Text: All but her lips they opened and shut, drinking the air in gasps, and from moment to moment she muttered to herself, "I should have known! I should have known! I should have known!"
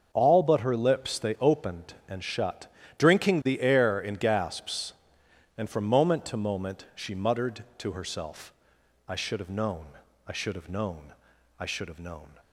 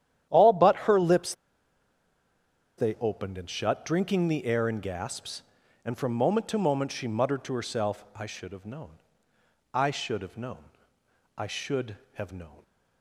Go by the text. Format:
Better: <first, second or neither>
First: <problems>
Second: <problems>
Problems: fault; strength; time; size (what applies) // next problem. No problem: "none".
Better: first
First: starts louder than the rest; until 1.1 s; 6.5 dB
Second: starts louder than the rest; strong; until 2.8 s; 10.5 dB // pauses between "lips" and "they"; strong; at 1.3 s; 1.4 s long